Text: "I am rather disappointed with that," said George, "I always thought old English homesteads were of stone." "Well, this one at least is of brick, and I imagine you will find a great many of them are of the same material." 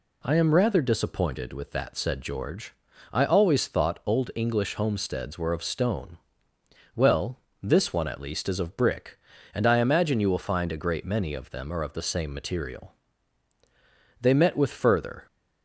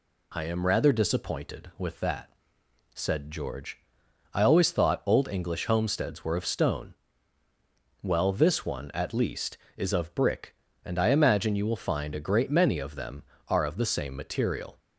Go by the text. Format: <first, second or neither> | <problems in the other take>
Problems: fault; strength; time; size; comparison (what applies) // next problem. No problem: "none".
second | goes on to say "They met with further"; noticeable; from 14.2 s on; 1.0 s long